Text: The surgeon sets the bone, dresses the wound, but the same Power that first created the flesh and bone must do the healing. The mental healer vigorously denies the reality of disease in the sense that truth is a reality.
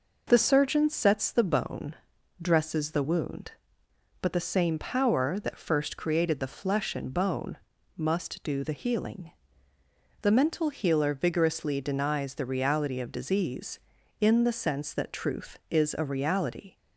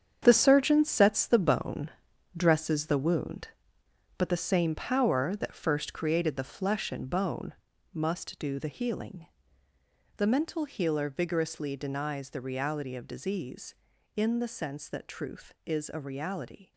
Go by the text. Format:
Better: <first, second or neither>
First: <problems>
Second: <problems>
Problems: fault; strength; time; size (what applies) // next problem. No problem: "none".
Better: first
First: pauses between "bone" and "must"; at 7.5 s; 0.40 s long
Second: gets quieter; strong; throughout; 10.5 dB // pauses between "bone" and "must"; at 7.5 s; 0.40 s long